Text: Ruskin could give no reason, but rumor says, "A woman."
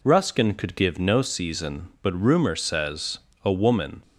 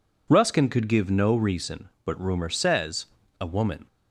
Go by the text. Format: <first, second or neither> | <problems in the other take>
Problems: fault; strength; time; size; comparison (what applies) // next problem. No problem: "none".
second | says "season" for "reason"; at 1.2 s